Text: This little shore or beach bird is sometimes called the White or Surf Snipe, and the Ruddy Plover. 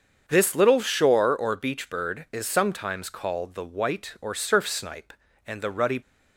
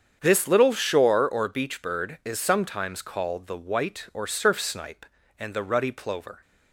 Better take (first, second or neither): second